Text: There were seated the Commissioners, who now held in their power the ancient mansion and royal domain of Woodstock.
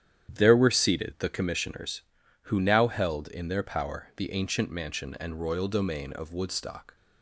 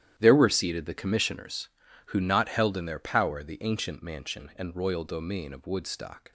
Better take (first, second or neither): first